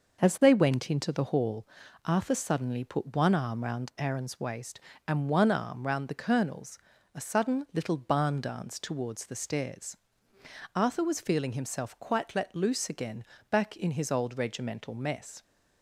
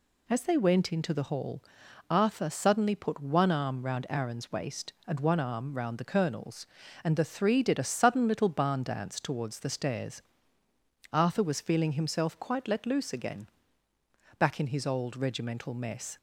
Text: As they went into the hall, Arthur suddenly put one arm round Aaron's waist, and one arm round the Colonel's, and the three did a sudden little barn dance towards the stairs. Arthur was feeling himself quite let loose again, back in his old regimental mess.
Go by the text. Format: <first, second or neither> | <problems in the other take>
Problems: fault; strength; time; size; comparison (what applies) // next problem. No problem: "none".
second | skips "and the three did"; at 6.9 s